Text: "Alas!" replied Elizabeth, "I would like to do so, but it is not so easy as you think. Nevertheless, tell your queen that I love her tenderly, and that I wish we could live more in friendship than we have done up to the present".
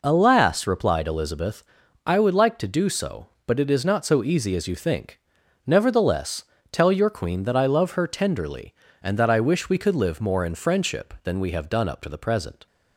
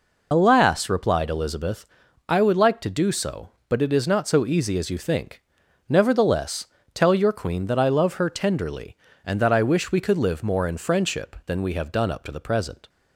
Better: first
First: none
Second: loses the start of "Alas"; at 0.3 s; 65 ms

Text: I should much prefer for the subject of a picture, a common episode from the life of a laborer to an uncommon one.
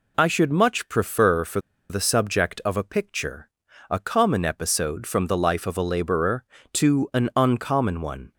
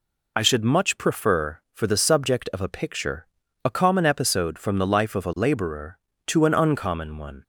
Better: second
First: pauses between "for" and "the"; slight; at 1.5 s; 0.31 s long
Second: none

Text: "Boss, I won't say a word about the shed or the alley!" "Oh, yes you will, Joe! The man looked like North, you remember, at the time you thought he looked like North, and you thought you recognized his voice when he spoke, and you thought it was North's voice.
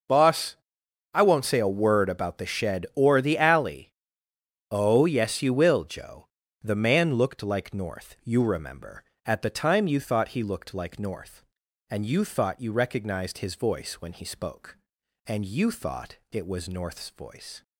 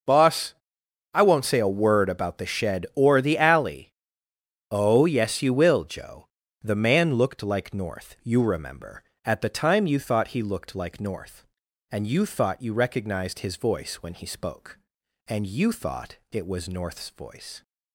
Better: neither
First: none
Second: none

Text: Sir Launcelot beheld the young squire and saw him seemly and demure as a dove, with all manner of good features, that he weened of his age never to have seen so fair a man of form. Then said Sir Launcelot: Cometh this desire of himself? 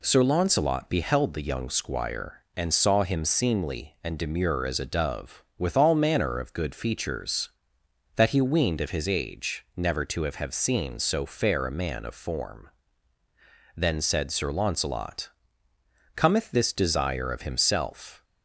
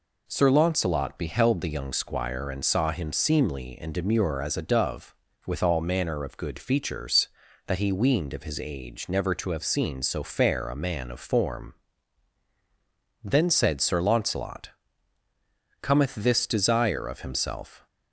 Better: second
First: says "have" twice; at 10.3 s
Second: none

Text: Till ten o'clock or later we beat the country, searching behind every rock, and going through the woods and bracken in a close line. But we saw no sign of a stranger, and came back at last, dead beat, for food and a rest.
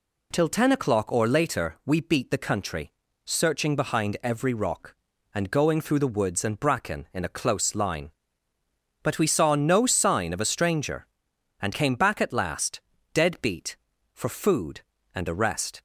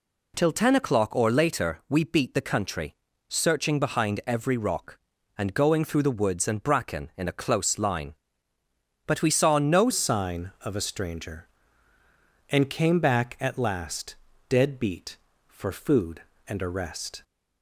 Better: first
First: none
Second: changes voice at "sign"; from 9.9 s on; 7.3 s long

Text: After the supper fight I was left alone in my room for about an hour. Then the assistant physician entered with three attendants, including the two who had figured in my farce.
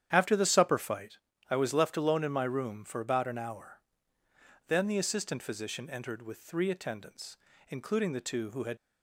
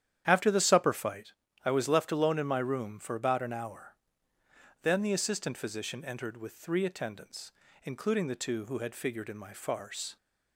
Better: second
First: starts louder than the rest; strong; until 1.1 s; 9.5 dB // pauses between "fight" and "I"; slight; at 1.1 s; 0.32 s long // stops before "figured in my farce"; at 8.7 s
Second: starts louder than the rest; strong; until 1.2 s; 10 dB // pauses between "fight" and "I"; slight; at 1.3 s; 0.32 s long

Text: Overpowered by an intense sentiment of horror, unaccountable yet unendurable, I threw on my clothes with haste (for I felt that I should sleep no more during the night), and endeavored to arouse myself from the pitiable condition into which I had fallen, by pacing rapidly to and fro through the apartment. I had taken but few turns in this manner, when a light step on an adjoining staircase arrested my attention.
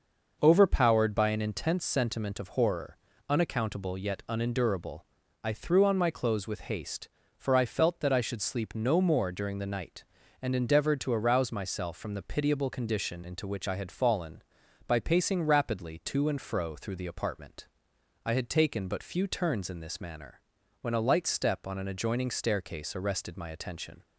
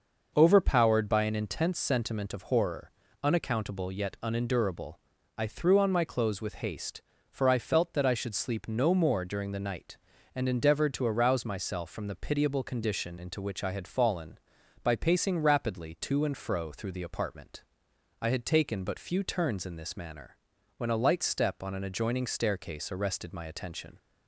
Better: neither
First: none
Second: none

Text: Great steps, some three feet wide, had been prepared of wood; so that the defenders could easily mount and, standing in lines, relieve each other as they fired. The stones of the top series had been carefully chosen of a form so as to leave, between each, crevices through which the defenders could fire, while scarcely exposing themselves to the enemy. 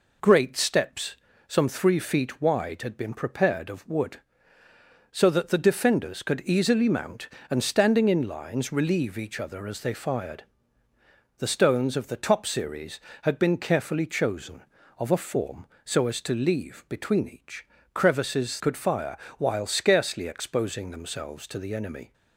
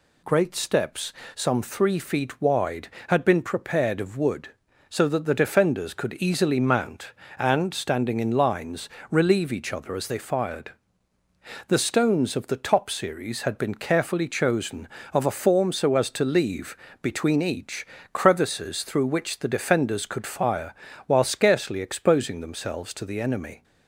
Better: second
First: skips "through which the defenders"; at 18.5 s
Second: none

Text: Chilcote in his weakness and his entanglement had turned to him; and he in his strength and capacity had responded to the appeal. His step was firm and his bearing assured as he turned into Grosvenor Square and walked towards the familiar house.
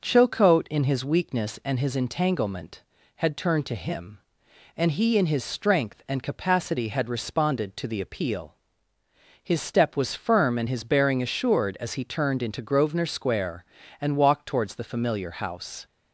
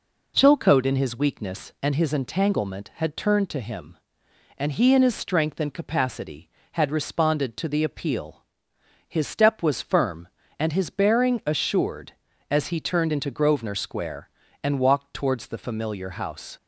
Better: neither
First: none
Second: none

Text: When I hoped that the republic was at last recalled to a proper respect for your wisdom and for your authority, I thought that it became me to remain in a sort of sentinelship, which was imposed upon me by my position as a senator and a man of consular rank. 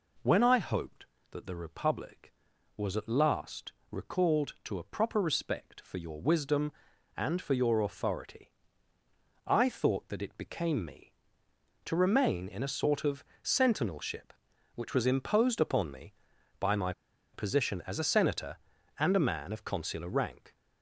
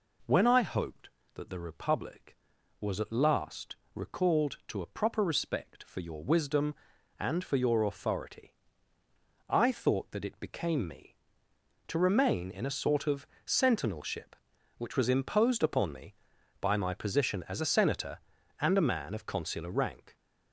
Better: second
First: pauses between "last" and "recalled"; slight; at 3.7 s; 0.20 s long // pauses between "of" and "sentinelship"; slight; at 13.2 s; 0.20 s long // pauses between "my" and "position"; at 16.9 s; 0.41 s long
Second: pauses between "last" and "recalled"; slight; at 3.7 s; 0.20 s long // pauses between "of" and "sentinelship"; slight; at 13.2 s; 0.20 s long

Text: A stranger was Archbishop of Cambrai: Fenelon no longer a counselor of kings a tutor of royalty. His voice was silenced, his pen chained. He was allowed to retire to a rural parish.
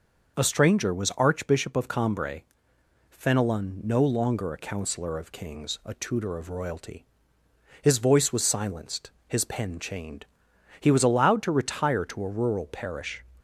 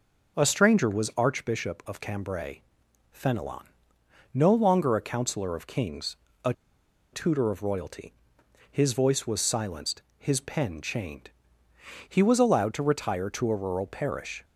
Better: first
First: none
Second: pauses between "Fenelon" and "no"; noticeable; at 3.6 s; 0.68 s long // pauses between "kings" and "a"; slight; at 6.1 s; 0.28 s long // pauses between "a" and "tutor"; noticeable; at 6.5 s; 0.60 s long

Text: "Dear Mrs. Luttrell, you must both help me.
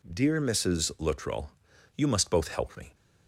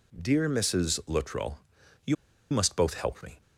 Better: first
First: none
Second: pauses between "you" and "must"; at 2.1 s; 0.37 s long

